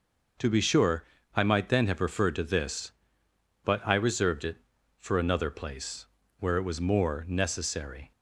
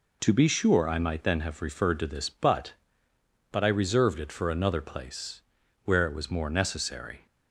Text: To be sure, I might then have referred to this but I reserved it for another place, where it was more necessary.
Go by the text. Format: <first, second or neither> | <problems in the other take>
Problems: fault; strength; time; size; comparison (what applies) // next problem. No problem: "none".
first | says "but" twice; at 3.5 s